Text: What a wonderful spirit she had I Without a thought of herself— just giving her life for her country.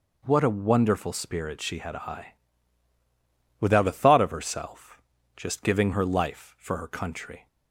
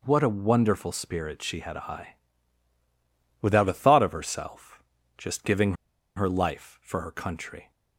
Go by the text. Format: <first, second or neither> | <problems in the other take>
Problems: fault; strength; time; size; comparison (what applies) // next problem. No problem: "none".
first | pauses between "I" and "Without"; strong; at 2.1 s; 1.2 s long; strong in the first // pauses between "giving" and "her"; at 5.7 s; 0.42 s long